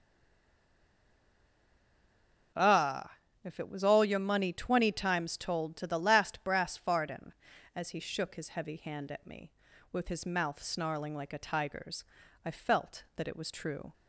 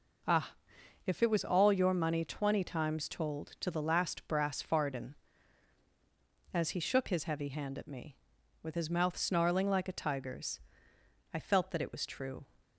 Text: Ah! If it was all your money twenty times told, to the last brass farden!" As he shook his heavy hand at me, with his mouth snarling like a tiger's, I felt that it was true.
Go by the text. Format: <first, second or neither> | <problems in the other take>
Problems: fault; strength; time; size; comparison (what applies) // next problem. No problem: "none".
second | stays silent before the first word; strong; until 2.5 s; 2.5 s long